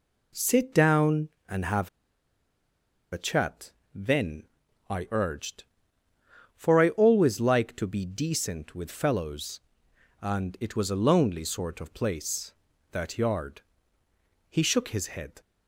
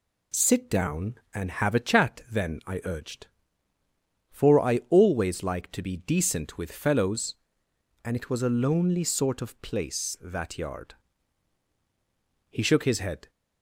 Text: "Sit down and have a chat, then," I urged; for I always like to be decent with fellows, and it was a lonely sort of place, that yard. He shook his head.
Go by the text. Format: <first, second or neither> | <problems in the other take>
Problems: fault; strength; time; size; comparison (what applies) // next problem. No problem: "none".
second | pauses between "have" and "a"; strong; at 1.8 s; 1.2 s long